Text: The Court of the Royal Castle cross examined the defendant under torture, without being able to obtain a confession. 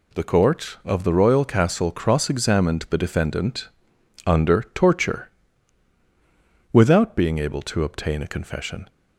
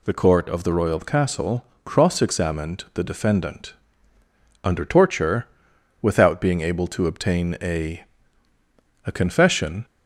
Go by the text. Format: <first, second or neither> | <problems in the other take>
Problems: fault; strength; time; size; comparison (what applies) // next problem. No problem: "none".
first | pauses between "Castle" and "cross"; slight; at 1.6 s; 0.22 s long // pauses between "defendant" and "under"; noticeable; at 3.7 s; 0.92 s long; noticeable in the first // says "a" twice; at 9.0 s